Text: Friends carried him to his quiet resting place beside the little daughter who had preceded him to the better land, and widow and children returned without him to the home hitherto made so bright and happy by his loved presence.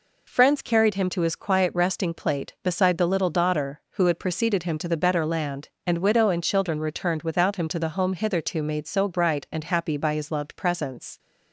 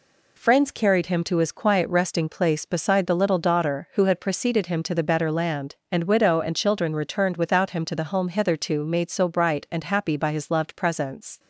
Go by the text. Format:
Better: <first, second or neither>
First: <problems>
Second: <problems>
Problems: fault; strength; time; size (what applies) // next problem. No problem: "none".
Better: second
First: says "plate" for "place"; at 2.1 s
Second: none